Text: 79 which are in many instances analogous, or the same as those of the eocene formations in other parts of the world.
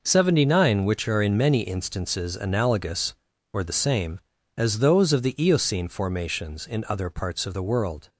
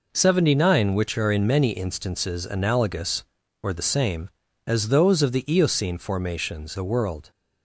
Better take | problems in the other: first | skips "in other parts of"; at 6.7 s

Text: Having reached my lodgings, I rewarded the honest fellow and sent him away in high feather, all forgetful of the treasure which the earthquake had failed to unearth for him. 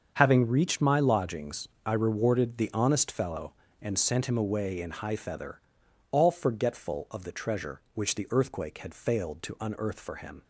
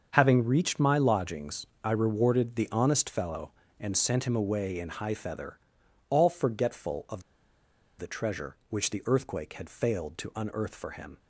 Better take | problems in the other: first | starts louder than the rest; until 1.1 s; 7 dB; also in the first // pauses between "of" and "the"; noticeable; at 7.2 s; 0.75 s long

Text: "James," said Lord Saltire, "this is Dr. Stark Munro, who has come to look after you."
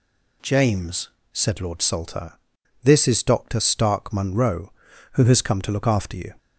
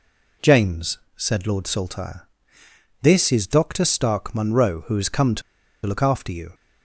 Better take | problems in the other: first | pauses between "to" and "look"; at 5.4 s; 0.44 s long

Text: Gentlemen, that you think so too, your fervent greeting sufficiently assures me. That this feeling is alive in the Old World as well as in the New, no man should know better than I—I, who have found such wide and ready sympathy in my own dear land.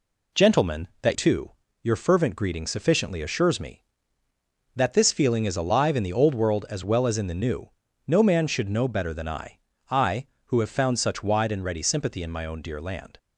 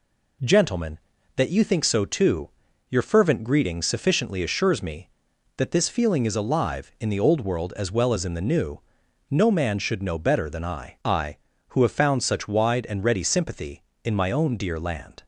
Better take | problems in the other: second | skips "you think so"; at 1.1 s

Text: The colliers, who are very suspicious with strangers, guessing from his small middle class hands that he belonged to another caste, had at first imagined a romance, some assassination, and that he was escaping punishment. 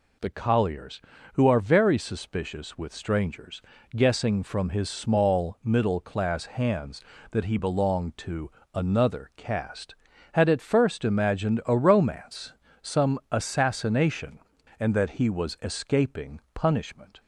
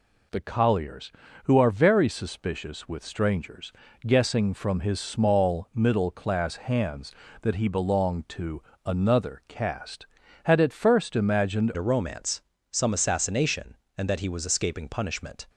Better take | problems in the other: first | pauses between "to" and "another"; slight; at 8.6 s; 0.24 s long; slight in the first // changes voice at "a"; from 11.7 s on; 3.7 s long

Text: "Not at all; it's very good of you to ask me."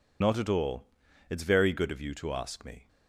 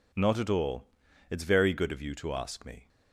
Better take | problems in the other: second | loses the start of "Not"; at 0.2 s; 65 ms

